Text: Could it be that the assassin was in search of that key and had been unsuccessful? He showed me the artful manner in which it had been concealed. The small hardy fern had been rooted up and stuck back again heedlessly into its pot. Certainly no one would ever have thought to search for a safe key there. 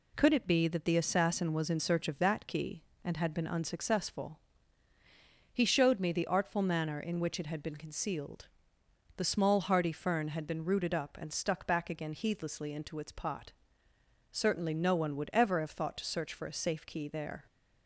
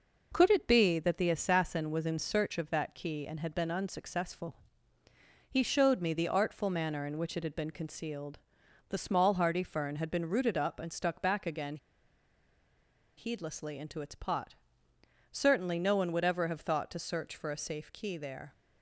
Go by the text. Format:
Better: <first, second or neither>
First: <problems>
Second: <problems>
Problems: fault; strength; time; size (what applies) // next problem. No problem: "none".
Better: first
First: none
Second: pauses between "again" and "heedlessly"; strong; at 11.7 s; 1.4 s long